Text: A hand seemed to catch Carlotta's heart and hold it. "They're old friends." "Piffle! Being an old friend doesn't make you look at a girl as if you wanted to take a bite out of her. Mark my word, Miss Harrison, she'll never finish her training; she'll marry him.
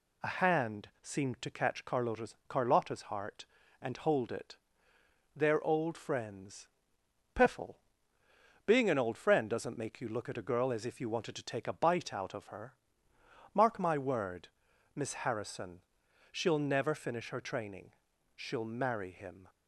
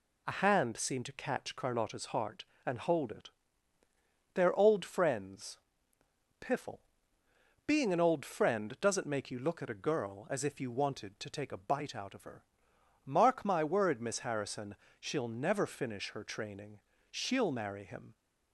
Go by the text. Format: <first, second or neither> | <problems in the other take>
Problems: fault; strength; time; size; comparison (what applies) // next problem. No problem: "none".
second | says "Carlotta's" twice; at 2.4 s